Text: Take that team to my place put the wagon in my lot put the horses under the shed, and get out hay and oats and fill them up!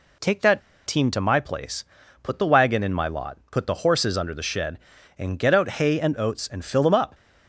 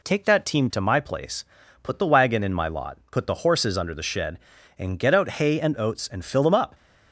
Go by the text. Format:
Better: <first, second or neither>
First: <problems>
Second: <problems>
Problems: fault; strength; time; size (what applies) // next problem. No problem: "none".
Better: second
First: pauses between "that" and "team"; slight; at 0.6 s; 0.25 s long // pauses between "place" and "put"; at 1.8 s; 0.38 s long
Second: pauses between "place" and "put"; at 1.4 s; 0.38 s long